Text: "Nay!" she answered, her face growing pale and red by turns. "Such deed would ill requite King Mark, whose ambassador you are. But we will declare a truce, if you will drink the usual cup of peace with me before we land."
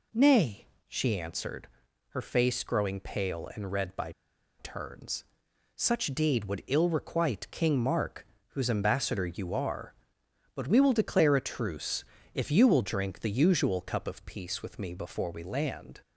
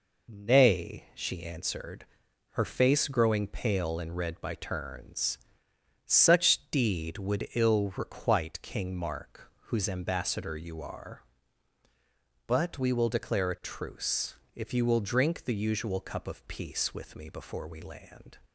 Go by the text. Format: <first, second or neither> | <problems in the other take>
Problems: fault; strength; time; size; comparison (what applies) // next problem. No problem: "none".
second | pauses between "by" and "turns"; noticeable; at 4.1 s; 0.48 s long